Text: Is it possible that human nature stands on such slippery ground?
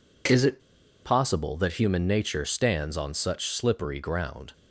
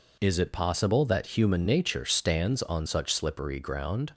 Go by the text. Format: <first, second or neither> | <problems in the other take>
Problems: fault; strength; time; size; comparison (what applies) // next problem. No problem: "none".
second | pauses between "it" and "possible"; noticeable; at 0.5 s; 0.46 s long